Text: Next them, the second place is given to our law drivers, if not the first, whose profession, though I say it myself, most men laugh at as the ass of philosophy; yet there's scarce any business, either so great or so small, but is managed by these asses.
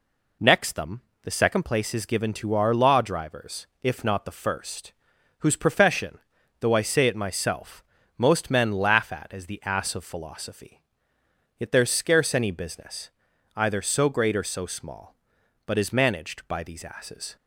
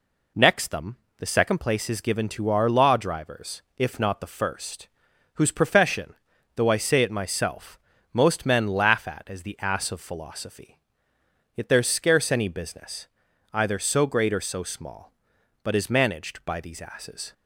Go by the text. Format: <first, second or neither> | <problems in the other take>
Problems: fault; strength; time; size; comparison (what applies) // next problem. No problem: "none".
neither | none